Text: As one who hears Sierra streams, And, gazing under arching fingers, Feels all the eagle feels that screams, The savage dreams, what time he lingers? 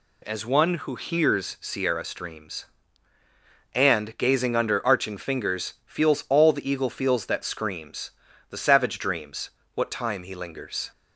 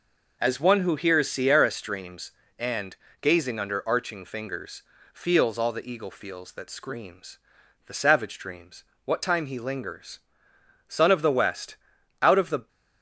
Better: first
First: none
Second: goes on to say "Son of the West out of the"; strong; from 10.8 s on; 1.8 s long

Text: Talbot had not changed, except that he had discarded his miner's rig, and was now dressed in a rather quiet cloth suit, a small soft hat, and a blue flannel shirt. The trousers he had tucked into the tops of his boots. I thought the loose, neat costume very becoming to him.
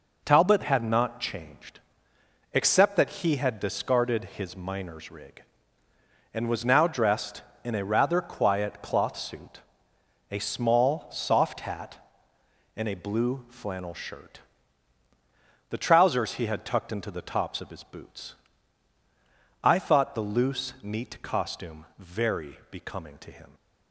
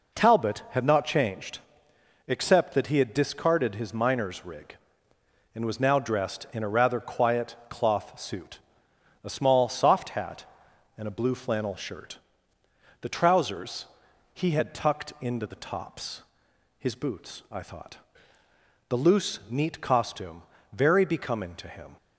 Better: first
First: none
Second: pauses between "trousers" and "he"; noticeable; at 13.8 s; 0.46 s long // skips "of"; at 16.5 s // pauses between "thought" and "the"; noticeable; at 17.9 s; 0.90 s long // pauses between "costume" and "very"; slight; at 20.4 s; 0.30 s long

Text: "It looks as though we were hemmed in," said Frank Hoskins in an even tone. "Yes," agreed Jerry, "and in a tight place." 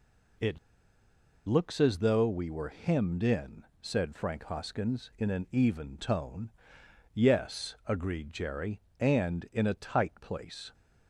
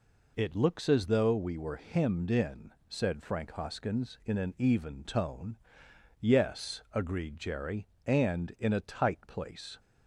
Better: second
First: pauses between "It" and "looks"; noticeable; at 0.5 s; 0.88 s long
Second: none

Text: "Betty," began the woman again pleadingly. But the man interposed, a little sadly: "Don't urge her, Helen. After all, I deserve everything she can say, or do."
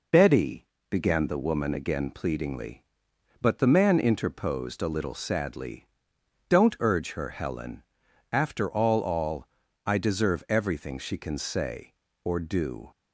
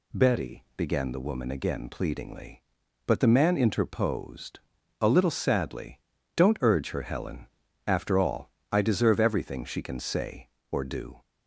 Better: second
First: says "all" twice; at 9.0 s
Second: none

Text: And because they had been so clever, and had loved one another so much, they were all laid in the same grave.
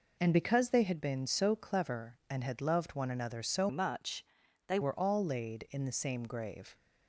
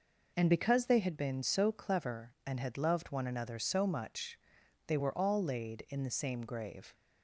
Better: second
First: changes voice from "much" to "they"; from 3.6 to 4.7 s; 1.1 s long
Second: none

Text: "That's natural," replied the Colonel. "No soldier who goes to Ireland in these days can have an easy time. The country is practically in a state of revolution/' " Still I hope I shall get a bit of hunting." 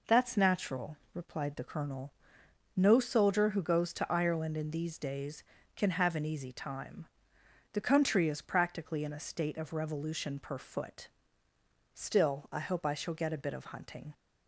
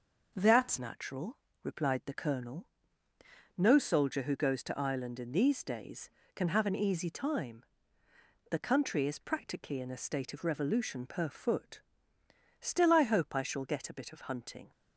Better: first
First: none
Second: starts louder than the rest; noticeable; until 1.3 s; 6 dB // changes voice at "natural"; from 0.7 s on; 14.0 s long

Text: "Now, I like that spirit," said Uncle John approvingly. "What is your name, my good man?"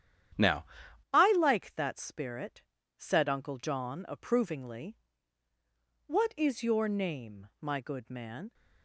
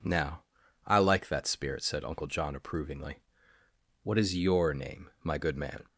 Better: second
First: starts louder than the rest; strong; until 1.8 s; 9.5 dB // changes voice at "I"; from 1.1 s on; 7.4 s long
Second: none

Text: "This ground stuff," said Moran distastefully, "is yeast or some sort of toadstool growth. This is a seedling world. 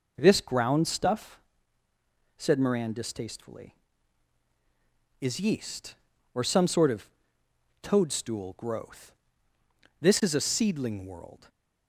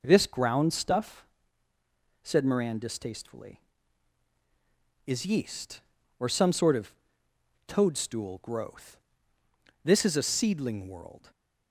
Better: neither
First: pauses between "of" and "toadstool"; noticeable; at 7.0 s; 0.72 s long // stays silent after the last word; slight; from 11.3 s on; 0.5 s long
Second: pauses between "of" and "toadstool"; noticeable; at 6.9 s; 0.72 s long // stays silent after the last word; slight; from 11.1 s on; 0.6 s long

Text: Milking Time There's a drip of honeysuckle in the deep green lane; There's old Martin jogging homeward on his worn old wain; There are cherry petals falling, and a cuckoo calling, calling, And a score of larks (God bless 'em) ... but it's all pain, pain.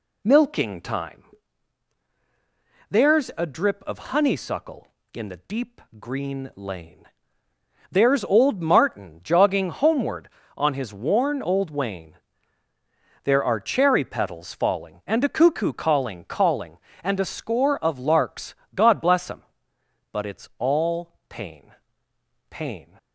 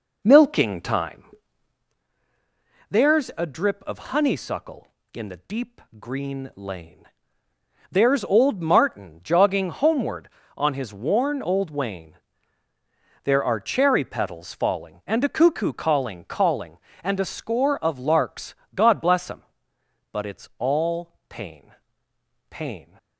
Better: first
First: pauses between "Time" and "There's"; strong; at 1.2 s; 1.6 s long // pauses between "deep" and "green"; slight; at 5.7 s; 0.18 s long // pauses between "all" and "pain"; slight; at 21.1 s; 0.16 s long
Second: starts louder than the rest; noticeable; until 2.1 s; 4 dB // pauses between "Time" and "There's"; strong; at 1.2 s; 1.6 s long // pauses between "deep" and "green"; slight; at 5.7 s; 0.18 s long // pauses between "all" and "pain"; slight; at 21.1 s; 0.16 s long

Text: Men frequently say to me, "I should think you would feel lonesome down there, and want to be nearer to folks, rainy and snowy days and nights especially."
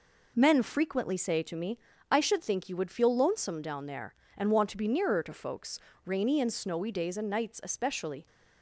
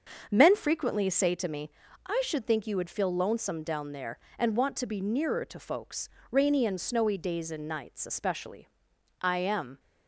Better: first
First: none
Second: starts louder than the rest; until 1.3 s; 6.5 dB // goes on to say "I am"; from 9.1 s on; 0.60 s long

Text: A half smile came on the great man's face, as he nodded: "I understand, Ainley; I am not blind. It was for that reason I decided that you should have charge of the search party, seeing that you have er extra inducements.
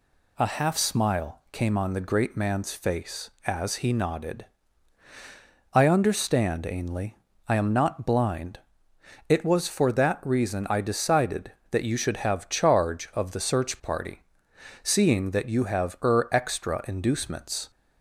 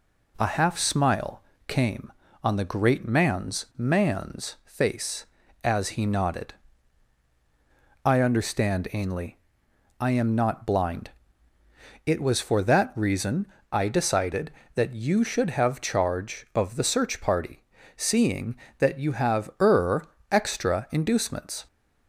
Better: first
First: none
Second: pauses between "smile" and "came"; slight; at 1.4 s; 0.26 s long // says "man's" twice; at 3.7 s // pauses between "reason" and "I"; slight; at 13.4 s; 0.24 s long // pauses between "er" and "extra"; slight; at 20.0 s; 0.24 s long

